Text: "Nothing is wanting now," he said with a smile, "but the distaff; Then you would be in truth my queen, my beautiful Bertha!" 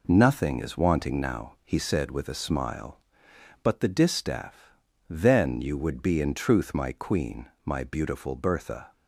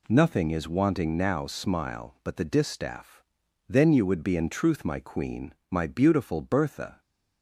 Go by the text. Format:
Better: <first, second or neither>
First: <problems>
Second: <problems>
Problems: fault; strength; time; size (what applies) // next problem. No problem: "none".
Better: first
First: none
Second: skips "he said with a"; at 1.4 s